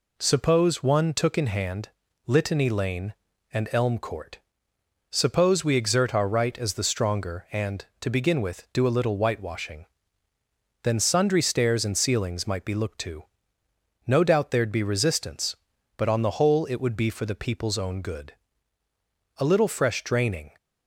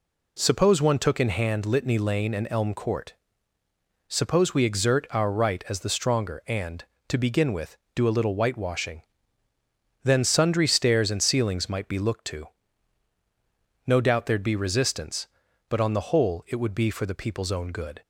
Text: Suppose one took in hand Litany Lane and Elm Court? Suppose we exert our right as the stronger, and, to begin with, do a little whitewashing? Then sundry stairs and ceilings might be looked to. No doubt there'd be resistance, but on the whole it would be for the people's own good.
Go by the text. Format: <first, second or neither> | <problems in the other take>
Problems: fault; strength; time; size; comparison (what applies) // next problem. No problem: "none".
second | pauses between "hand" and "Litany"; slight; at 1.9 s; 0.36 s long // goes on to say "A little fresh draining"; noticeable; from 19.3 s on; 1.1 s long